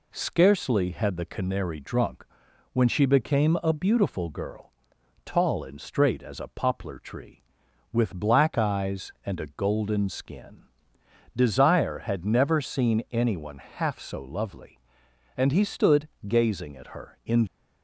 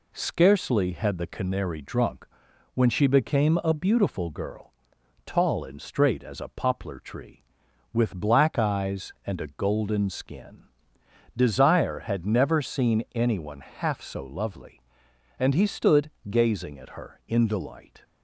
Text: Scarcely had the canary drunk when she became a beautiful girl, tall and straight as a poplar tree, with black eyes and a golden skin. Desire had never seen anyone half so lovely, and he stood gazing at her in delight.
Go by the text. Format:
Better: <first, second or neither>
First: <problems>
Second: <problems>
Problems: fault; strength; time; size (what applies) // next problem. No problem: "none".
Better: second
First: pauses between "drunk" and "when"; noticeable; at 2.2 s; 0.48 s long // pauses between "stood" and "gazing"; slight; at 16.0 s; 0.20 s long // stops before "delight"; at 17.4 s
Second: pauses between "drunk" and "when"; noticeable; at 2.2 s; 0.48 s long // pauses between "stood" and "gazing"; slight; at 16.0 s; 0.20 s long